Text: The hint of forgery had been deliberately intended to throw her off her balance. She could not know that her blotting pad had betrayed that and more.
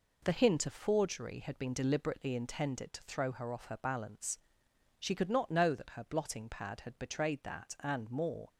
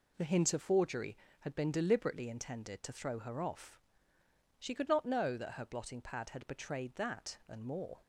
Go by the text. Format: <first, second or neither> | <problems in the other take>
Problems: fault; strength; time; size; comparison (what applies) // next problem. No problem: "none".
first | skips "her balance"; at 4.2 s